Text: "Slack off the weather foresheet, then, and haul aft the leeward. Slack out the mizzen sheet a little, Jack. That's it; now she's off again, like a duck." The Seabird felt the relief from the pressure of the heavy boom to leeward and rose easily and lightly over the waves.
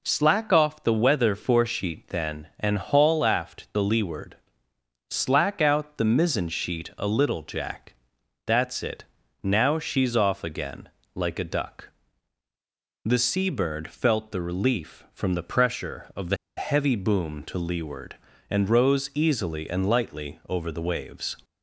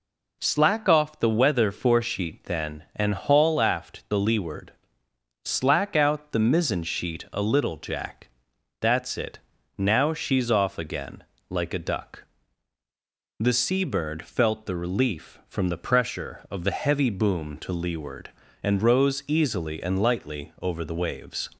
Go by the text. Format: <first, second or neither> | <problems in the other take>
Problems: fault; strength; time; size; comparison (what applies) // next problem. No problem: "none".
second | pauses between "the" and "heavy"; slight; at 16.3 s; 0.20 s long